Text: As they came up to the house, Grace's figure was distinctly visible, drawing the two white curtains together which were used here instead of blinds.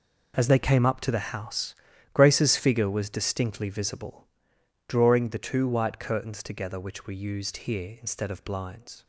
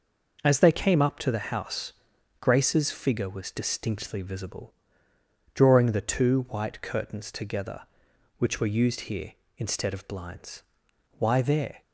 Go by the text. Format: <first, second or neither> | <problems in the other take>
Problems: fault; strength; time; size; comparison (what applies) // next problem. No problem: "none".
first | goes on to say "Why there"; noticeable; from 11.1 s on; 0.64 s long